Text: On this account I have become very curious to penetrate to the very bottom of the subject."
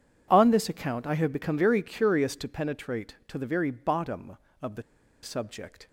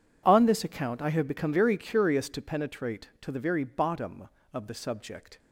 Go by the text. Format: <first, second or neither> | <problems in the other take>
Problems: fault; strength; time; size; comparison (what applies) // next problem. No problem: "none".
second | pauses between "the" and "subject"; at 4.8 s; 0.40 s long